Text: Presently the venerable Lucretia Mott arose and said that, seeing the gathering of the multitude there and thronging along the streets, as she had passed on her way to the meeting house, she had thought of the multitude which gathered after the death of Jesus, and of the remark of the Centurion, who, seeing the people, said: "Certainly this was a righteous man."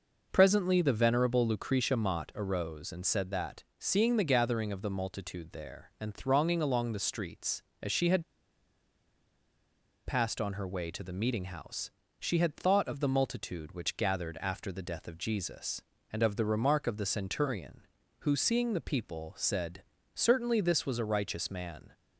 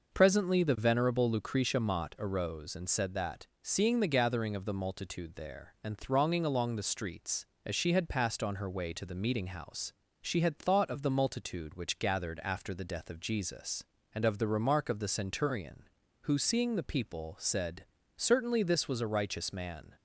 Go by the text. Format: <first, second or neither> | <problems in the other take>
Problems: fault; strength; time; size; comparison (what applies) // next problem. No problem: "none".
second | pauses between "had" and "passed"; strong; at 8.2 s; 1.8 s long